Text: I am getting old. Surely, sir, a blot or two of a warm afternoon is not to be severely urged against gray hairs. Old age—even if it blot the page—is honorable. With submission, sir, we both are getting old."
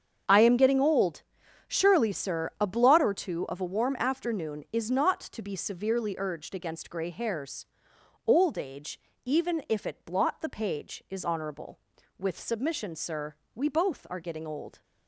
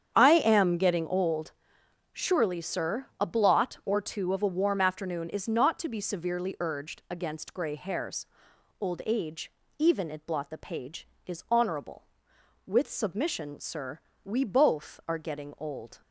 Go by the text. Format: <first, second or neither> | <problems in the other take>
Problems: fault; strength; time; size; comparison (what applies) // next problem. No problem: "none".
first | starts louder than the rest; strong; until 1.1 s; 8 dB; strong in the first // skips "if"; at 10.1 s